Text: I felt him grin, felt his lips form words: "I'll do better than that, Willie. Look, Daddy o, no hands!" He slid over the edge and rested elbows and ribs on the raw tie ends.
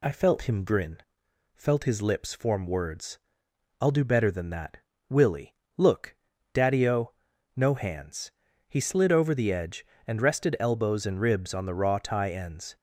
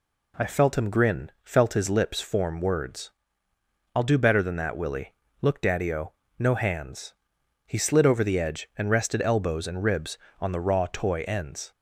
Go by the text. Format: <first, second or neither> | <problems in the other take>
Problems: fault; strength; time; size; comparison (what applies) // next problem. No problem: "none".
first | says "toy" for "tie"; at 10.9 s